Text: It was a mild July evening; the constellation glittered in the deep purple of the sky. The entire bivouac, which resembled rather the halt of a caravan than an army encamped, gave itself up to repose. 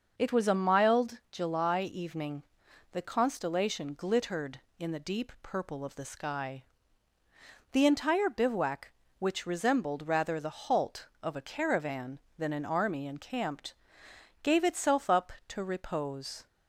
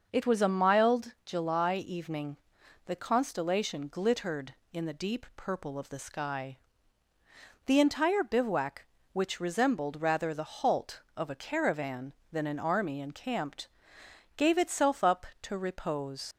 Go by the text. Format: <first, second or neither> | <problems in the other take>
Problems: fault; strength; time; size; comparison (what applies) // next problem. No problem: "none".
first | starts louder than the rest; noticeable; until 1.1 s; 6 dB; noticeable in the first // leaves "repose" unfinished; at 16.3 s; 85 ms